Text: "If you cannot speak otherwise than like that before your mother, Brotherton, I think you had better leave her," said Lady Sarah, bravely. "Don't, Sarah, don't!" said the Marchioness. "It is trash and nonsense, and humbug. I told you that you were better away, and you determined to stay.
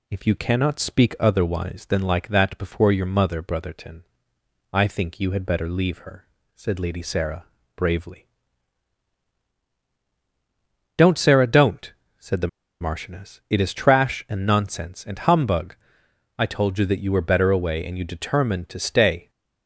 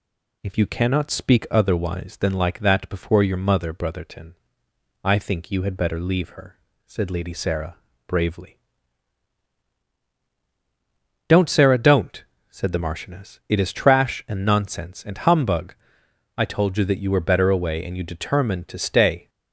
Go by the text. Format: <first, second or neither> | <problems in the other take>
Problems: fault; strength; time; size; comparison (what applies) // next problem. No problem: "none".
second | pauses between "the" and "Marchioness"; slight; at 12.4 s; 0.33 s long